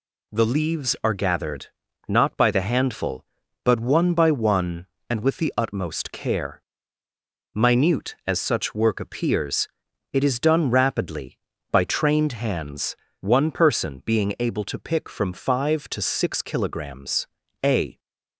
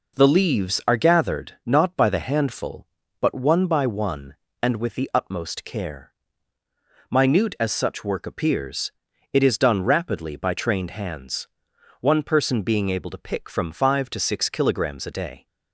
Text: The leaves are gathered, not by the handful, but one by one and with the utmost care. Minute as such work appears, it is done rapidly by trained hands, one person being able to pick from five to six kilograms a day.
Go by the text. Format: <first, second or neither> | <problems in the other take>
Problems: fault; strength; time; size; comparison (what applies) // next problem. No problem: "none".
second | pauses between "kilograms" and "a"; at 17.2 s; 0.38 s long // stops before "day"; at 17.9 s